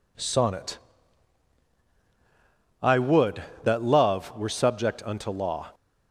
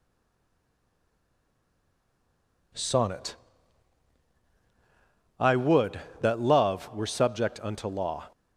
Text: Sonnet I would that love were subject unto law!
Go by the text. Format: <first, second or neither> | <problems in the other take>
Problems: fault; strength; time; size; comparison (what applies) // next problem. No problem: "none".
first | stays silent before the first word; strong; until 2.7 s; 2.7 s long // pauses between "Sonnet" and "I"; strong; at 3.3 s; 2.0 s long; strong in the first